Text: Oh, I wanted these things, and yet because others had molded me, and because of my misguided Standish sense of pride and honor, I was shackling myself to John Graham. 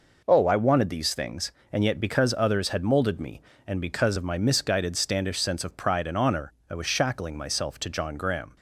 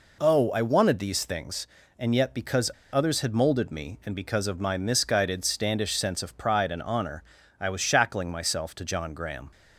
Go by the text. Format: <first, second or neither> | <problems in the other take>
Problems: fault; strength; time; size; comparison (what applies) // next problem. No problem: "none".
first | pauses between "because" and "others"; slight; at 2.7 s; 0.20 s long